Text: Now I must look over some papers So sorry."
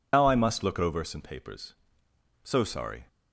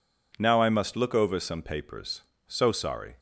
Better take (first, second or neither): second